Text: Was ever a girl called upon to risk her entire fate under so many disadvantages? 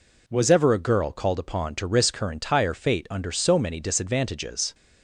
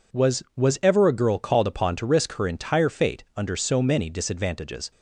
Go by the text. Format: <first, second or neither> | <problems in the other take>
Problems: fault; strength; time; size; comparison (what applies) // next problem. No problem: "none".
first | says "Was" twice; at 0.5 s